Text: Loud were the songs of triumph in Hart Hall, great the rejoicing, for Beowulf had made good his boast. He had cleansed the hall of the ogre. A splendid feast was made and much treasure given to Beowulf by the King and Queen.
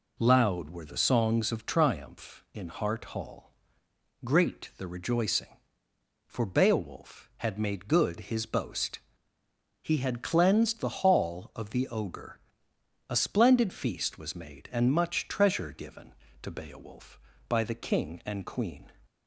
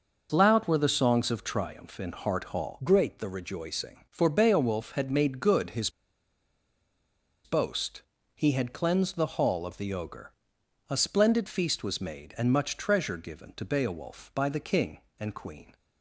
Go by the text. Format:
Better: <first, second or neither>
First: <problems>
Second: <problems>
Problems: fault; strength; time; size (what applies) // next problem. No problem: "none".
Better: first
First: none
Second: pauses between "his" and "boast"; strong; at 5.8 s; 1.5 s long